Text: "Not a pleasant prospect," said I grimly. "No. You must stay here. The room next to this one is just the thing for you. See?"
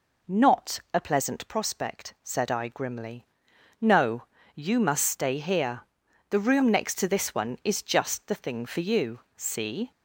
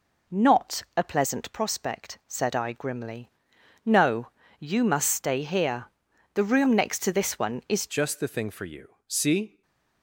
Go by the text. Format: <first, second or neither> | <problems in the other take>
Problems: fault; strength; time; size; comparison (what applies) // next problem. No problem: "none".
first | changes voice at "just"; from 7.8 s on; 1.8 s long // stays silent after the last word; slight; from 9.4 s on; 0.6 s long